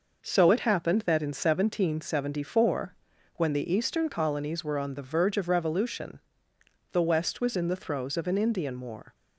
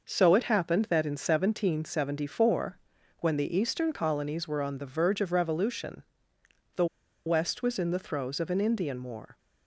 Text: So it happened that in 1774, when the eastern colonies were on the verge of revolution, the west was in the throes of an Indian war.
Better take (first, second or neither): first